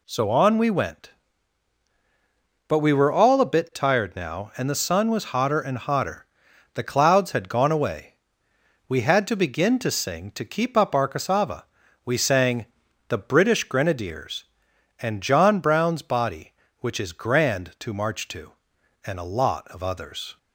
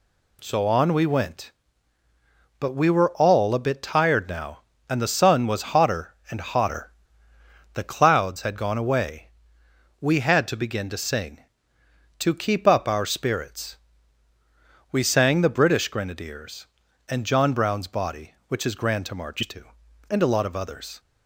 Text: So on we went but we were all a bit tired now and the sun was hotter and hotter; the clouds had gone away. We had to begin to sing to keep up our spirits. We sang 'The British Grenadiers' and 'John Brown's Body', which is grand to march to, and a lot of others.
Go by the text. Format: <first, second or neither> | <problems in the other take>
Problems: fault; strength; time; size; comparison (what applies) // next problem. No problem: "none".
second | says "cassava" for "spirits"; at 11.0 s // pauses between "sang" and "The"; at 12.6 s; 0.42 s long